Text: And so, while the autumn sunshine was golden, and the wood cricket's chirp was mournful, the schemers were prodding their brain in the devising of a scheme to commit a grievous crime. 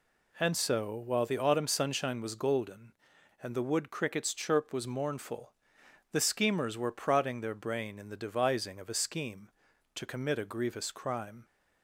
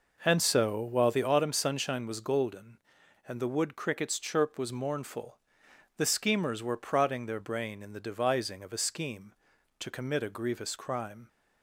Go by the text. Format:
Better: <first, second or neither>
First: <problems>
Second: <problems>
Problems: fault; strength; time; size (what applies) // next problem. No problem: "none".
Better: first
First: none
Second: starts louder than the rest; noticeable; until 1.4 s; 5 dB